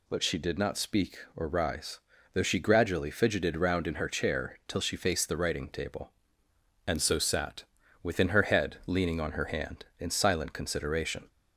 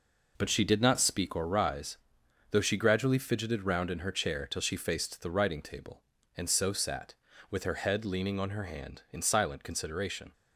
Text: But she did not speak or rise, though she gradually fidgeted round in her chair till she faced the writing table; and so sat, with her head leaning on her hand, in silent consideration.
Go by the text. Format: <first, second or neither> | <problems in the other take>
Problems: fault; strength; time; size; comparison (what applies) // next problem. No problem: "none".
second | says "within" for "with"; at 8.0 s